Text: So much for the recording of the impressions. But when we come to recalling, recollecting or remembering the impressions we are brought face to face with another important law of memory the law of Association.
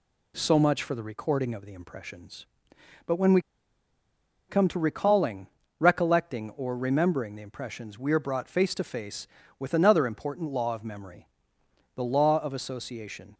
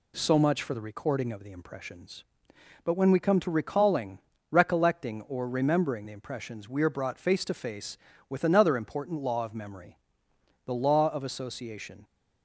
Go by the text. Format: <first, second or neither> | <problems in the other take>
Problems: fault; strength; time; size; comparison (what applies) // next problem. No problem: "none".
second | pauses between "we" and "come"; at 3.3 s; 1.0 s long // pauses between "memory" and "the"; noticeable; at 11.2 s; 0.70 s long; noticeable in the second